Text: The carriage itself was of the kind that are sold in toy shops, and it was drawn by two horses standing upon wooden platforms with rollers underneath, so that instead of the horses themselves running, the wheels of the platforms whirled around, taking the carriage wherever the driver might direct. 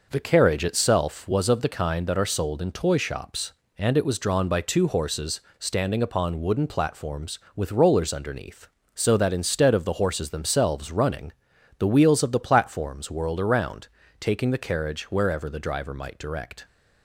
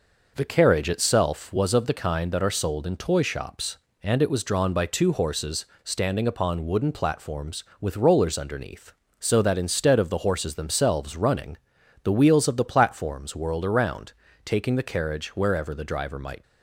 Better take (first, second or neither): first